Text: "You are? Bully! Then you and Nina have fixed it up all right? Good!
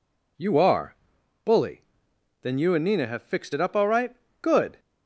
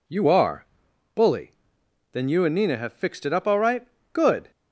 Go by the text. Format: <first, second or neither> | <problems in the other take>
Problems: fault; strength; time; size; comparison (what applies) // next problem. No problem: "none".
neither | none